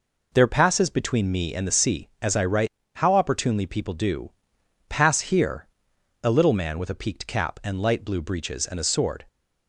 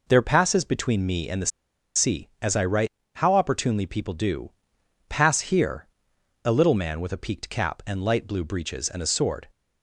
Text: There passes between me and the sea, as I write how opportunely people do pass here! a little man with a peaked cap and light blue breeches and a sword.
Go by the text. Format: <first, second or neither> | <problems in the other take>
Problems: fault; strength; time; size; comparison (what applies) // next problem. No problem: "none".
first | pauses between "the" and "sea"; noticeable; at 1.5 s; 0.47 s long // pauses between "write" and "how"; slight; at 2.8 s; 0.26 s long; slight in the first // pauses between "do" and "pass"; noticeable; at 4.5 s; 0.56 s long; noticeable in the first